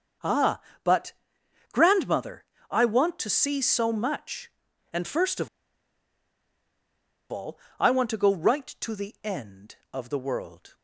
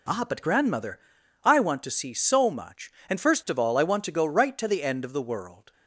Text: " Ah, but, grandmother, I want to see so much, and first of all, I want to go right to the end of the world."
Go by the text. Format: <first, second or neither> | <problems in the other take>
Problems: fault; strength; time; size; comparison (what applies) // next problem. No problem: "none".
second | starts louder than the rest; until 2.0 s; 6.5 dB // pauses between "of" and "all"; strong; at 5.4 s; 1.8 s long